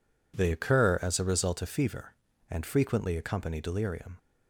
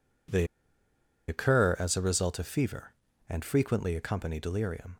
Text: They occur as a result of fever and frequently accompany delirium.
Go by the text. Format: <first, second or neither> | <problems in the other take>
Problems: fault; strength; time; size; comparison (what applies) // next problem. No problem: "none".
first | pauses between "They" and "occur"; noticeable; at 0.4 s; 0.83 s long